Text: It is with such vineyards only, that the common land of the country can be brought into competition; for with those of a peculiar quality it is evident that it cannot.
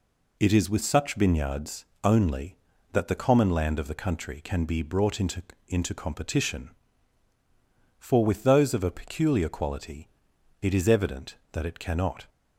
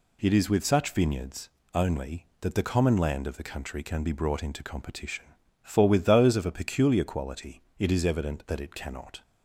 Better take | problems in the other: second | pauses between "vineyards" and "only"; slight; at 1.8 s; 0.20 s long; slight in the second // says "into" twice; at 5.6 s // pauses between "quality" and "it"; noticeable; at 10.0 s; 0.54 s long; slight in the second

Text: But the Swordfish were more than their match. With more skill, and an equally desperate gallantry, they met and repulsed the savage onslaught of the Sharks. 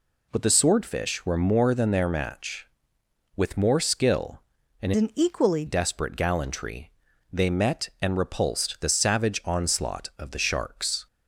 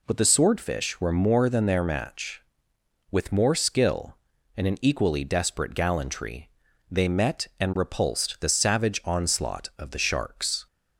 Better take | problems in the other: second | changes voice from "an" to "equally"; from 4.9 to 5.6 s; 0.7 s long

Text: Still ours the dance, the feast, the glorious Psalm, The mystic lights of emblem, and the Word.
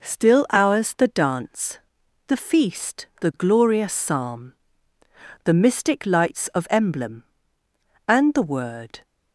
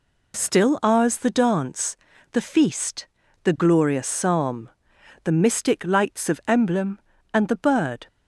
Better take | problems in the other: first | says "Bird" for "Word"; at 7.5 s

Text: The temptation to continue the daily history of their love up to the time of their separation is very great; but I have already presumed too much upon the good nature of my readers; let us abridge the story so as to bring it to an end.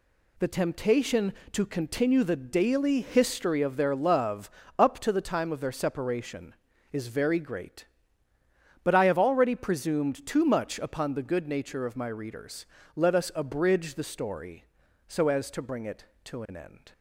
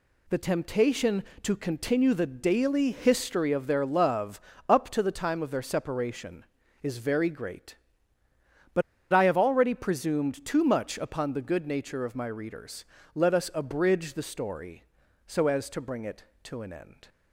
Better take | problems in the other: first | pauses between "love" and "up"; slight; at 4.3 s; 0.28 s long; slight in the first // pauses between "but" and "I"; slight; at 8.8 s; 0.30 s long

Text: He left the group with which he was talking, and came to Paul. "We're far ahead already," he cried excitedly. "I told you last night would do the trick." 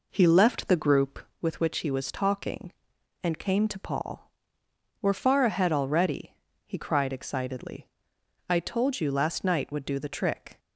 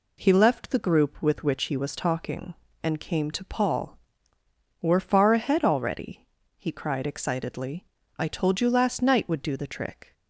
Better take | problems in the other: second | starts louder than the rest; noticeable; until 1.4 s; 4 dB

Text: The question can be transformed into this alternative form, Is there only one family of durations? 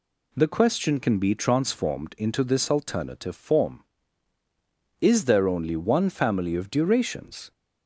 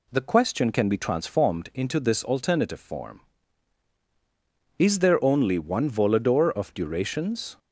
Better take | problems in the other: first | says "volador" for "family"; at 5.9 s

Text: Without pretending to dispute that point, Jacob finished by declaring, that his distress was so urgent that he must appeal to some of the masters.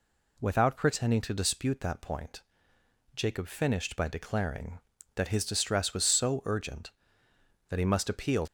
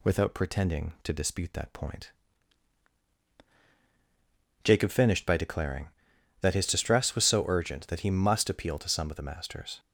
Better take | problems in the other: second | stops before "to some of the masters"; at 8.4 s

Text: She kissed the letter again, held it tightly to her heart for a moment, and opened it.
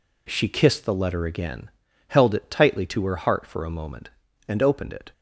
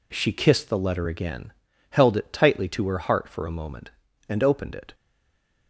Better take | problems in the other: first | stays silent after the last word; slight; from 4.9 s on; 0.7 s long

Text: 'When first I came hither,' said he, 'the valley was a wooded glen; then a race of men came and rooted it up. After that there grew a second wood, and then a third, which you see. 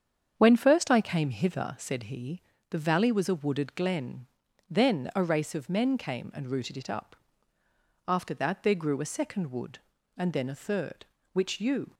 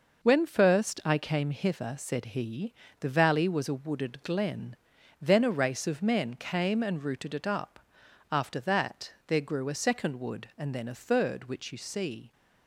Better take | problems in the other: second | starts louder than the rest; strong; until 1.3 s; 7.5 dB // stops before "see"; at 11.9 s

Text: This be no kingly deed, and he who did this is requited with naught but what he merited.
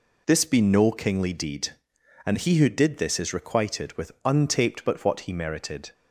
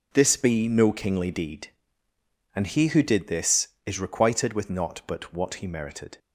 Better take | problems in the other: second | says "untaped" for "naught"; at 4.2 s

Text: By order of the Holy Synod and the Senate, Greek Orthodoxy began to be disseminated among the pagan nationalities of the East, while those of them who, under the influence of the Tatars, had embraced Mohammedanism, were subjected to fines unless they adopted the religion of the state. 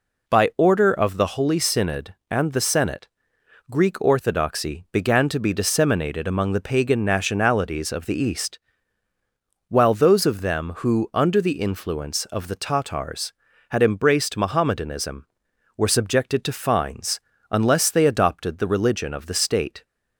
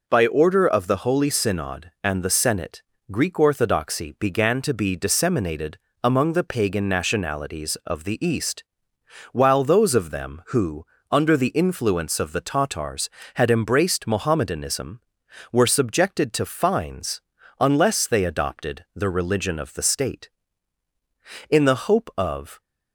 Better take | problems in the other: first | pauses between "disseminated" and "among"; slight; at 5.7 s; 0.26 s long // pauses between "fines" and "unless"; at 17.1 s; 0.38 s long; slight in the first // goes on to say "In the hope of"; noticeable; from 21.4 s on; 1.1 s long

